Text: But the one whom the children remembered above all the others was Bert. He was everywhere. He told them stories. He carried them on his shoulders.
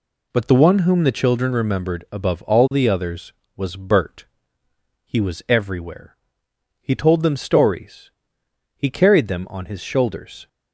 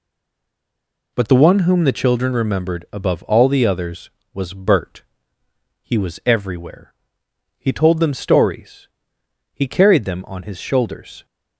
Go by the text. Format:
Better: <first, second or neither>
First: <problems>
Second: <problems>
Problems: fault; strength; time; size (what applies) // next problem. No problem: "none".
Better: first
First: none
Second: stays silent before the first word; until 1.1 s; 1.1 s long